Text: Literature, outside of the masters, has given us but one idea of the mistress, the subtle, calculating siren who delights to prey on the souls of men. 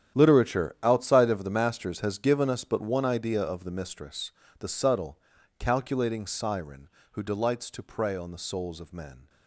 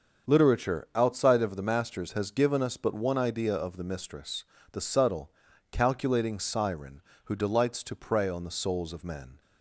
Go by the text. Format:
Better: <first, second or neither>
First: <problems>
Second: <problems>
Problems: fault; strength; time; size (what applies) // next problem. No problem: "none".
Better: second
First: gets quieter; strong; throughout; 15 dB // starts louder than the rest; strong; until 1.2 s; 10 dB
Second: starts louder than the rest; until 1.3 s; 7 dB